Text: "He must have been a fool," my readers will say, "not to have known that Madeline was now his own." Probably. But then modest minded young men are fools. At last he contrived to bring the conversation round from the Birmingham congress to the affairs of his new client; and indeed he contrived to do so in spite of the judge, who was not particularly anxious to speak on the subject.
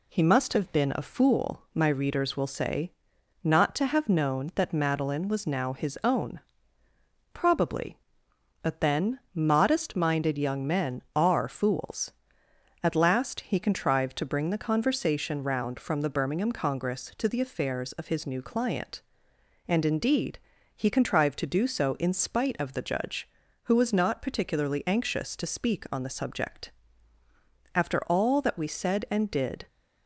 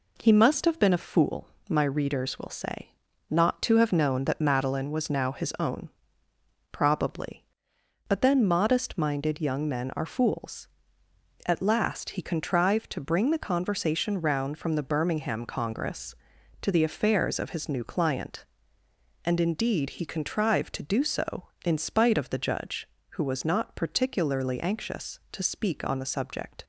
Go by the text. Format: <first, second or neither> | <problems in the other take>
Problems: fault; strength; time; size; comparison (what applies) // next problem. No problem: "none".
second | pauses between "indeed" and "he"; slight; at 20.4 s; 0.34 s long // goes on to say "After all that we said and did"; strong; from 27.7 s on; 1.9 s long